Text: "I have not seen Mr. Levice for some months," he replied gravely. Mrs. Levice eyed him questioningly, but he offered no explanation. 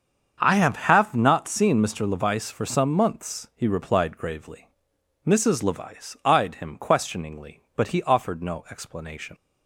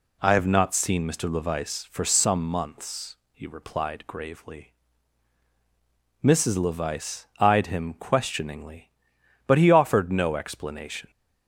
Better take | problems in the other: second | starts louder than the rest; strong; until 1.4 s; 7 dB // says "have" twice; at 0.7 s

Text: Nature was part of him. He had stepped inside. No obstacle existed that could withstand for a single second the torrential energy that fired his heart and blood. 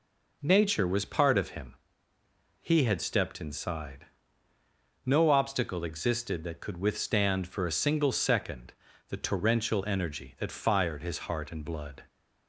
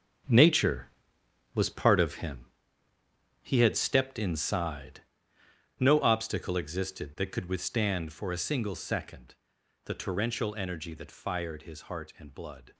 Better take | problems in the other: first | gets quieter; strong; throughout; 11 dB // pauses between "second" and "the"; noticeable; at 9.3 s; 0.50 s long; slight in the first

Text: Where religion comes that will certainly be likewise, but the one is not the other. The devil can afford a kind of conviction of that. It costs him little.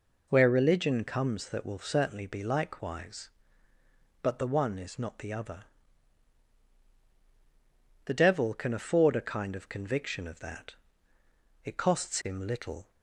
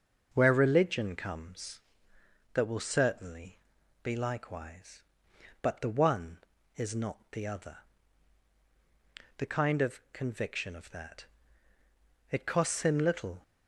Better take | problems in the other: first | starts louder than the rest; noticeable; until 1.3 s; 6 dB // pauses between "certainly" and "be"; at 3.5 s; 0.44 s long // skips "devil can afford a"; at 9.4 s

